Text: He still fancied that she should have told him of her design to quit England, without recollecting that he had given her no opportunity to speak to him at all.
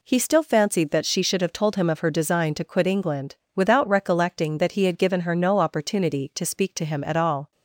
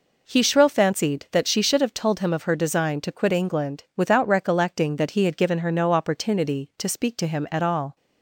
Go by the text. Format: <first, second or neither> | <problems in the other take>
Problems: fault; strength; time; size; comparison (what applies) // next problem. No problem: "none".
first | says "shrill" for "still"; at 0.4 s